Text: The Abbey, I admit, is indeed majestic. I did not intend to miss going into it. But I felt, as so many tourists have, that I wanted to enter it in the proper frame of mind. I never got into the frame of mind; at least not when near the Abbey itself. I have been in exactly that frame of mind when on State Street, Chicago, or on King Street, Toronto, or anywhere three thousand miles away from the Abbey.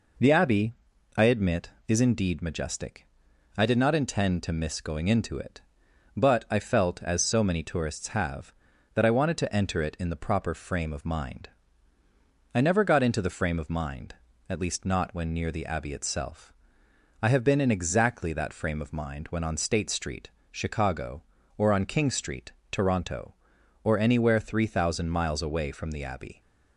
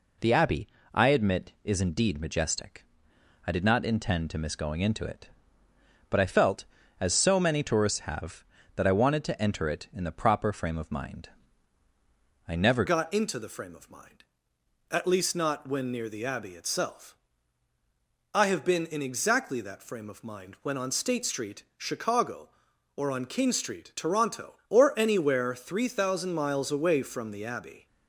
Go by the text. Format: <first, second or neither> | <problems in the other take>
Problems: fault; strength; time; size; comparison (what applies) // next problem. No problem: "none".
first | changes voice at "got"; from 12.8 s on; 15.0 s long